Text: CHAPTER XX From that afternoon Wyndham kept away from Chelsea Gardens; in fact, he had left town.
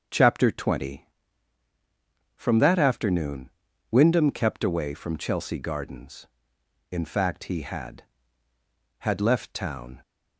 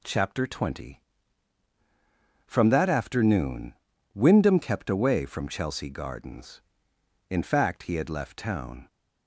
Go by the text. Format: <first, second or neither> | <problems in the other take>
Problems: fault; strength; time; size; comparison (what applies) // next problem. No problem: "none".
second | starts louder than the rest; until 2.4 s; 6.5 dB // pauses between "afternoon" and "Wyndham"; at 3.5 s; 0.40 s long; also in the second // says "had" twice; at 9.0 s